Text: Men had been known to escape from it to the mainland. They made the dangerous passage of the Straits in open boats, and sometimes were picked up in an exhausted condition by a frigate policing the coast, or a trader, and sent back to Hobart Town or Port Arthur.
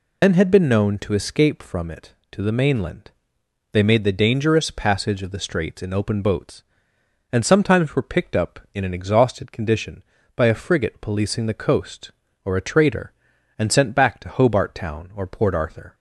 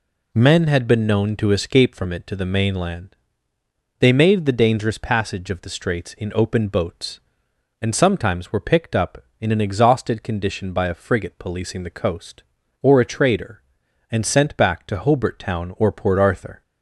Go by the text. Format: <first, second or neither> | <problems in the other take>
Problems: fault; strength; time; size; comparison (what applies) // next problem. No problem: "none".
second | loses the start of "Men"; at 0.2 s; 100 ms